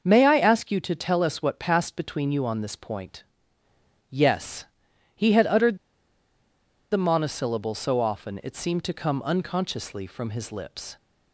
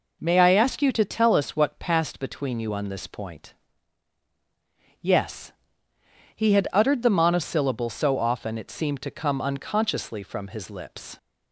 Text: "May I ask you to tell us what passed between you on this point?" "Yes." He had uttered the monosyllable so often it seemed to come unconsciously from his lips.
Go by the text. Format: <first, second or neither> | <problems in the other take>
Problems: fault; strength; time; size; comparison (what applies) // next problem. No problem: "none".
second | starts louder than the rest; until 1.0 s; 6.5 dB // pauses between "uttered" and "the"; at 5.7 s; 1.1 s long